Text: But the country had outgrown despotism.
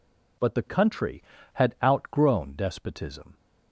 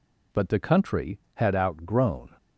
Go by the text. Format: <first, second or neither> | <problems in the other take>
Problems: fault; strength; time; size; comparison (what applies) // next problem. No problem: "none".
first | stops before "despotism"; at 2.3 s